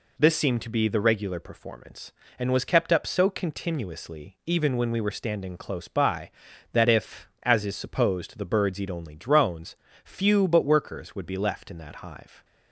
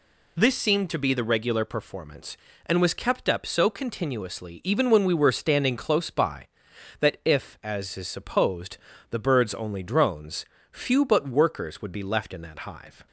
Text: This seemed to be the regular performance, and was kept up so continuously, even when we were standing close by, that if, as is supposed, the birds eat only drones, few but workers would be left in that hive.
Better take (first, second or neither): first